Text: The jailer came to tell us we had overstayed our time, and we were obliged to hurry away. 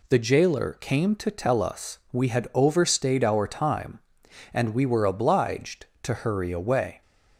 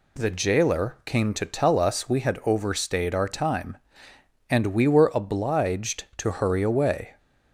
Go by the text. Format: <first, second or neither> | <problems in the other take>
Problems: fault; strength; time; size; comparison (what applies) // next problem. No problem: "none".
neither | none